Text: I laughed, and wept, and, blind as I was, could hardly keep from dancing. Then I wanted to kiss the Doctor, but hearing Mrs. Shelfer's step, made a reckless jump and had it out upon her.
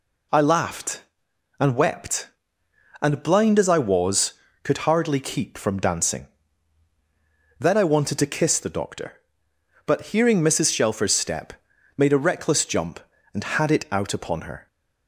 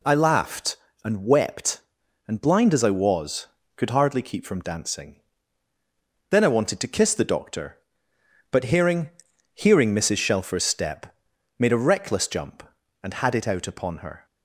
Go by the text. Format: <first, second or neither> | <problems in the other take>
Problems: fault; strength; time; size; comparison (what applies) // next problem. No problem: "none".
first | says "hearing" twice; at 9.5 s